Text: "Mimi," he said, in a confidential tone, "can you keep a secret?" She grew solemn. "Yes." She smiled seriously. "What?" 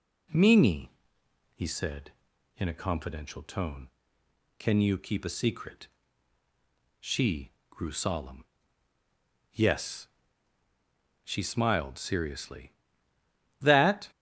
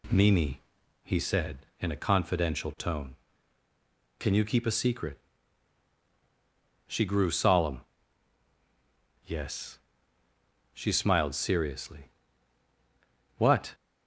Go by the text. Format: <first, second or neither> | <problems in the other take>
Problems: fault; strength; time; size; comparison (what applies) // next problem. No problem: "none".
second | pauses between "She" and "grew"; slight; at 7.5 s; 0.18 s long // says "That" for "What"; at 13.5 s